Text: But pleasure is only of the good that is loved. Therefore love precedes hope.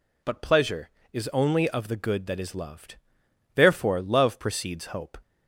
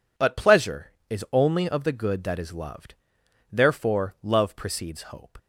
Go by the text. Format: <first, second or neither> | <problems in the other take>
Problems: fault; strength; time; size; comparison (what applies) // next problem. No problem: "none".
neither | none